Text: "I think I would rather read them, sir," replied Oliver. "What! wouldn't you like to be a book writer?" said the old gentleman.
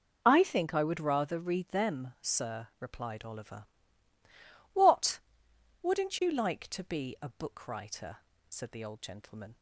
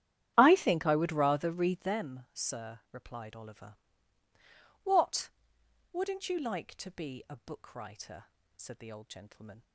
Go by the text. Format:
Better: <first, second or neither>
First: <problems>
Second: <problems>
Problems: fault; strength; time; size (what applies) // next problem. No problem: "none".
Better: first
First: none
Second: starts louder than the rest; strong; until 1.9 s; 11 dB